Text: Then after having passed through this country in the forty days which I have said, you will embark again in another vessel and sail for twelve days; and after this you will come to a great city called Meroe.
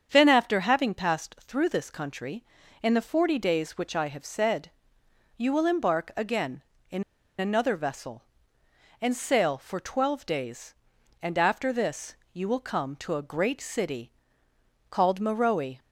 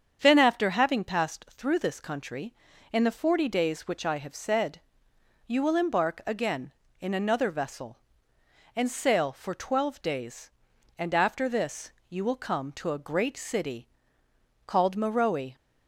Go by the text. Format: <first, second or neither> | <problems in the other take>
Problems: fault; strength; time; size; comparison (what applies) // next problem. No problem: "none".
second | starts louder than the rest; strong; until 1.1 s; 7.5 dB; strong in the second // pauses between "in" and "another"; slight; at 7.0 s; 0.35 s long // pauses between "this" and "you"; slight; at 12.1 s; 0.18 s long; slight in the second // pauses between "city" and "called"; noticeable; at 14.1 s; 0.80 s long; noticeable in the second